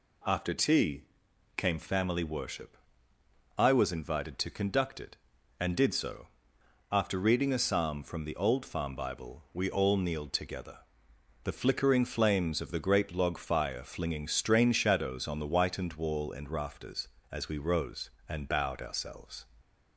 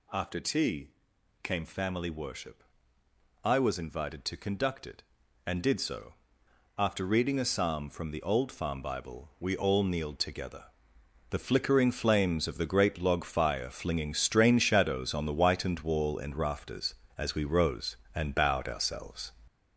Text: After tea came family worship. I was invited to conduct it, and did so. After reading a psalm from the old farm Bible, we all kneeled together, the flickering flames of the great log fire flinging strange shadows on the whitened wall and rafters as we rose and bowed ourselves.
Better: first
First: pauses between "tea" and "came"; noticeable; at 1.0 s; 0.54 s long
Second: gets louder; noticeable; throughout; 6 dB // pauses between "tea" and "came"; noticeable; at 0.8 s; 0.54 s long

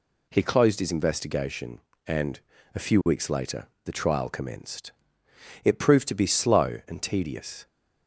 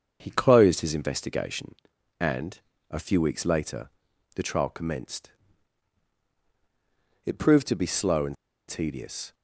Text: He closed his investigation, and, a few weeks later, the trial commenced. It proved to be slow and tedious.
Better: first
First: none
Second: starts louder than the rest; until 1.2 s; 7 dB // pauses between "and" and "tedious"; slight; at 8.3 s; 0.34 s long

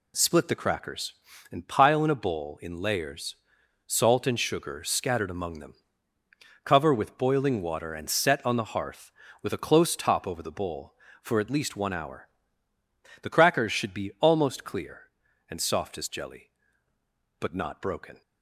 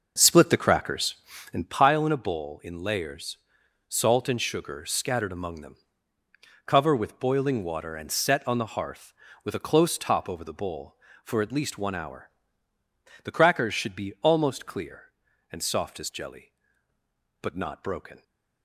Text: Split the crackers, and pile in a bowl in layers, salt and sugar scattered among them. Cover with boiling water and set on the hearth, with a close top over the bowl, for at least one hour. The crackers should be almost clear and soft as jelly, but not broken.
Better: first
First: none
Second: starts louder than the rest; noticeable; until 1.8 s; 6 dB

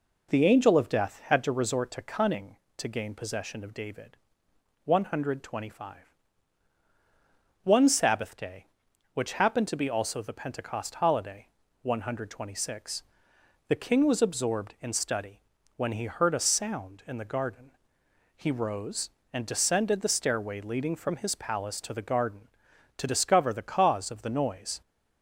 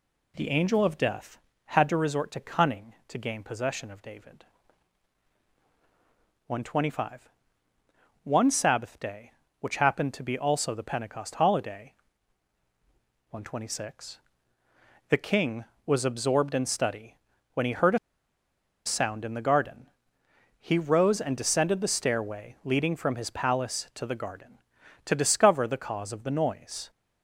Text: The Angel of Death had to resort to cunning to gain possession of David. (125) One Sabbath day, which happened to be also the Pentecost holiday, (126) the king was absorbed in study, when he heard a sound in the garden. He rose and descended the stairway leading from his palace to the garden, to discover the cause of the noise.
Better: first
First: none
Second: pauses between "a" and "sound"; noticeable; at 17.9 s; 0.87 s long

